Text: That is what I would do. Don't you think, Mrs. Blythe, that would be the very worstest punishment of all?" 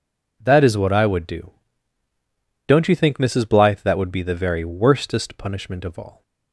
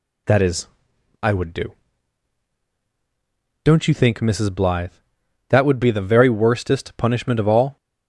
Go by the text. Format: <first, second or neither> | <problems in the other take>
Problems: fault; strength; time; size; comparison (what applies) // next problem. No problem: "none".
first | skips "what"; at 0.9 s